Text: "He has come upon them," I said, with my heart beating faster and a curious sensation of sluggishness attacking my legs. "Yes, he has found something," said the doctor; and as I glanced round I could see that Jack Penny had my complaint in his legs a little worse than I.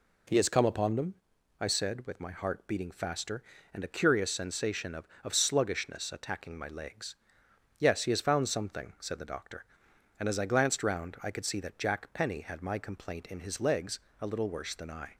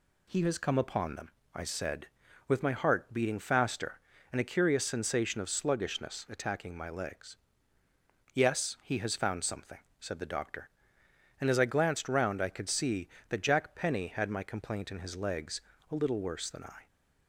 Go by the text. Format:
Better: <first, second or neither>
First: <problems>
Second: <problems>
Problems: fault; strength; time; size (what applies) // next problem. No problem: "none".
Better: second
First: says "of" twice; at 5.2 s // pauses between "legs" and "a"; slight; at 14.0 s; 0.20 s long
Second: pauses between "legs" and "a"; slight; at 15.6 s; 0.28 s long